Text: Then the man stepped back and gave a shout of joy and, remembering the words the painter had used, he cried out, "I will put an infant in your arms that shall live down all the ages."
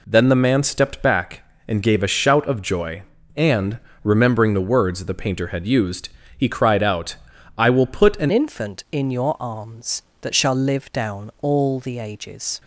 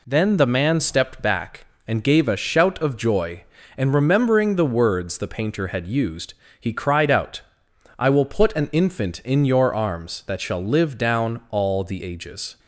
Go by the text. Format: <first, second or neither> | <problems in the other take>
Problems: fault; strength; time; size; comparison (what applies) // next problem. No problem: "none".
second | changes voice at "infant"; from 8.3 s on; 4.3 s long